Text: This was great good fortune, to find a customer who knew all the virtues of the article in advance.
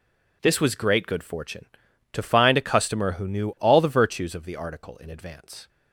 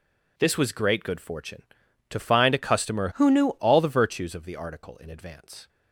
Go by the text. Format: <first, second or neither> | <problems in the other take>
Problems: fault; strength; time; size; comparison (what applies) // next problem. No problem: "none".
first | changes voice from "who" to "knew"; from 3.1 to 3.5 s; 0.4 s long